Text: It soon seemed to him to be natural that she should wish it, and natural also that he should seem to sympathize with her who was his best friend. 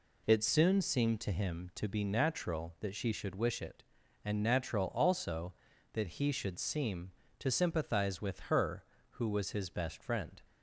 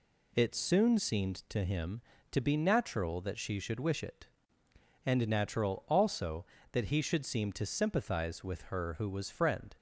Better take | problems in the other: first | skips "his best"; at 9.2 s

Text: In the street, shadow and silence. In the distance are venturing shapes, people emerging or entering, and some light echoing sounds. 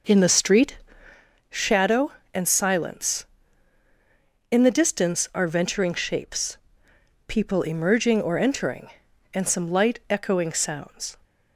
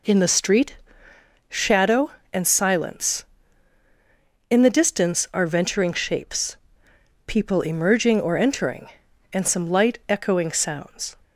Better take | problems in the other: second | starts louder than the rest; noticeable; until 1.2 s; 5.5 dB

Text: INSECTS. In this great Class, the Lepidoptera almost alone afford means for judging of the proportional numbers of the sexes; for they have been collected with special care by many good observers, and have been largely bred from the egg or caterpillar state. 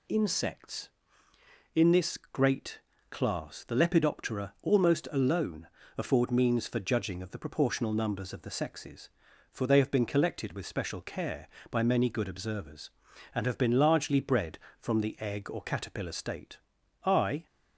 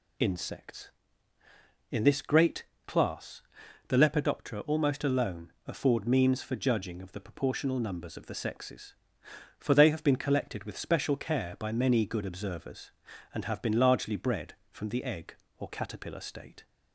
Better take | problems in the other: second | pauses between "great" and "Class"; slight; at 2.7 s; 0.32 s long; slight in the second // pauses between "alone" and "afford"; slight; at 5.6 s; 0.28 s long // goes on to say "I"; slight; from 17.0 s on; 0.40 s long

